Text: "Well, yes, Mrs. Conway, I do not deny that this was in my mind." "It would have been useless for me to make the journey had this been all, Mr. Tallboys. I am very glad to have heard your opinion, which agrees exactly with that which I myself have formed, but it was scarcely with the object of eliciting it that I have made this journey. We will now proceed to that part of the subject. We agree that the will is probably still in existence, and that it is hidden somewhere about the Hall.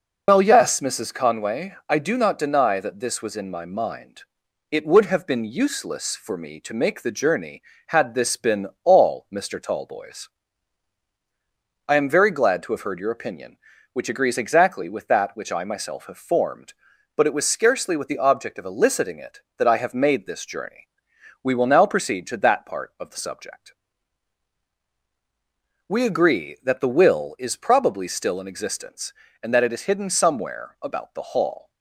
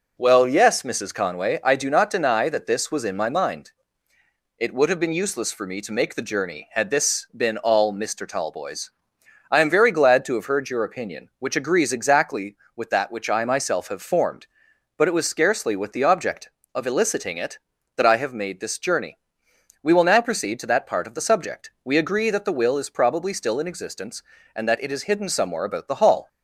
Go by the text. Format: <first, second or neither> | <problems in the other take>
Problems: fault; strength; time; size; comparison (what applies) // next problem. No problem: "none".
second | loses the start of "Well"; at 0.2 s; 105 ms // pauses between "been" and "all"; slight; at 8.6 s; 0.16 s long